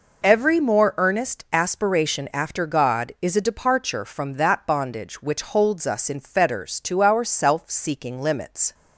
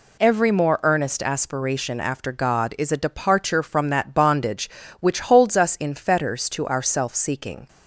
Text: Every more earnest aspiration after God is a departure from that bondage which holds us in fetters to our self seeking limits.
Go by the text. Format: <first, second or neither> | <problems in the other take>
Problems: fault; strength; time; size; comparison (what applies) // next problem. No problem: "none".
first | stops before "limits"; at 7.6 s